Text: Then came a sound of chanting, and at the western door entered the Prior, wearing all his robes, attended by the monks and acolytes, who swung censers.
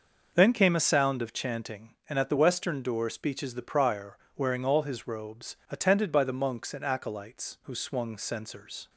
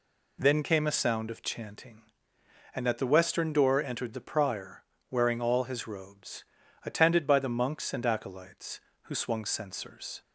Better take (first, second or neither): second